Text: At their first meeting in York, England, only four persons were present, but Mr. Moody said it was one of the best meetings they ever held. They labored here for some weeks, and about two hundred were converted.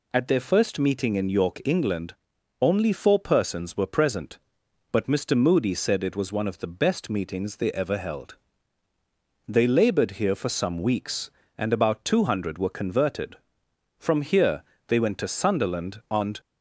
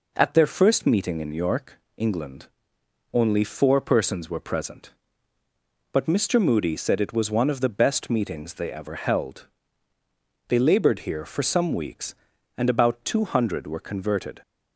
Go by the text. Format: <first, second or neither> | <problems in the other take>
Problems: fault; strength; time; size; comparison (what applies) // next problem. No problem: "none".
second | goes on to say "From here they went to Sunderland and"; strong; from 13.9 s on; 2.4 s long